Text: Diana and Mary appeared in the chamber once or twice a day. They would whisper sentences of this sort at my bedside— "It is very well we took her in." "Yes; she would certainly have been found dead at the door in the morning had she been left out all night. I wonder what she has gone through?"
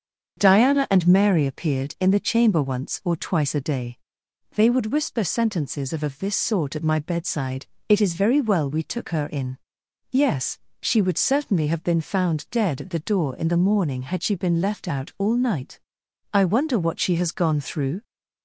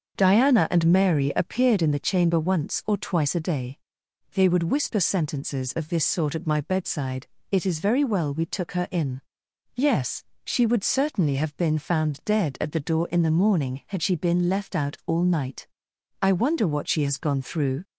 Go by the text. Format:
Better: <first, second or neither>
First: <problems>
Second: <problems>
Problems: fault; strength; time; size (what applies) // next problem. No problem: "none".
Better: second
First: starts louder than the rest; until 1.3 s; 7 dB // says "of" twice; at 6.0 s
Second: starts louder than the rest; until 1.2 s; 6.5 dB